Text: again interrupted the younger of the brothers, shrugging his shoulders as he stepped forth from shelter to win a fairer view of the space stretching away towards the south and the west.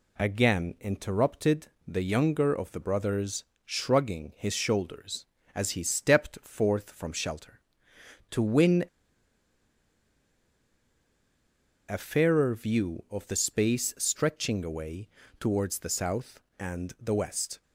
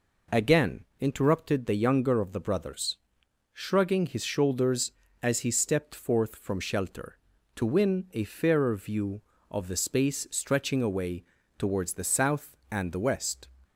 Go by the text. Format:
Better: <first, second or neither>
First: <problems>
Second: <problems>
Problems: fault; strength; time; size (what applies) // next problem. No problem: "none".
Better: second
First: pauses between "interrupted" and "the"; slight; at 1.6 s; 0.20 s long // pauses between "win" and "a"; strong; at 8.8 s; 3.0 s long // pauses between "away" and "towards"; slight; at 15.0 s; 0.32 s long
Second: pauses between "away" and "towards"; slight; at 11.2 s; 0.34 s long